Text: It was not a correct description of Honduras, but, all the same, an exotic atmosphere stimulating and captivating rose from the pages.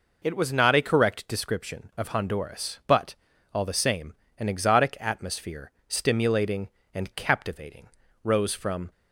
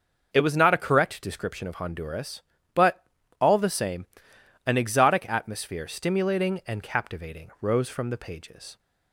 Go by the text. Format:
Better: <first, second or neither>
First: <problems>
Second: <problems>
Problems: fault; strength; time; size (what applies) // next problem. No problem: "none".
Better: second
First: pauses between "atmosphere" and "stimulating"; slight; at 5.7 s; 0.18 s long // pauses between "captivating" and "rose"; at 7.8 s; 0.38 s long // stops before "the pages"; at 8.9 s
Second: none